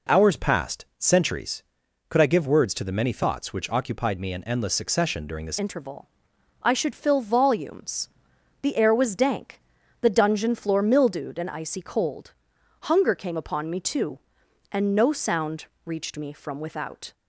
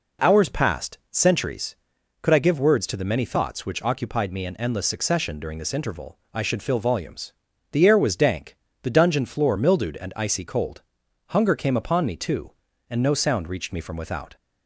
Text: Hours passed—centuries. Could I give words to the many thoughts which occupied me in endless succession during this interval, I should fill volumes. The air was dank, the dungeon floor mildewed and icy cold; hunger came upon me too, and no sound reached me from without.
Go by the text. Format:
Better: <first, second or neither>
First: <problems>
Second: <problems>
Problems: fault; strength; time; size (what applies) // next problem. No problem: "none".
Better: second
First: changes voice at "interval"; from 5.5 s on; 11.6 s long // pauses between "sound" and "reached"; slight; at 15.6 s; 0.20 s long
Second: none